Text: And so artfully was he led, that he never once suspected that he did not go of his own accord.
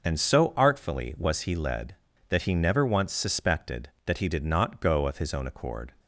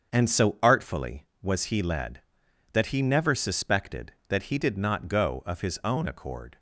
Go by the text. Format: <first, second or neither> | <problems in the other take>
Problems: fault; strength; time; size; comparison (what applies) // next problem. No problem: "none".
first | starts louder than the rest; until 1.1 s; 7 dB // skips "once"; at 3.3 s